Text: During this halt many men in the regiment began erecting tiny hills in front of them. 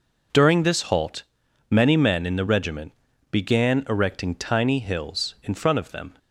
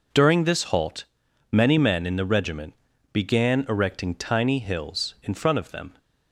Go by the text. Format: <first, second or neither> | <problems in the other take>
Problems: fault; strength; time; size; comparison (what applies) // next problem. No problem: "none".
neither | pauses between "halt" and "many"; noticeable; the same in both // pauses between "regiment" and "began"; the same in both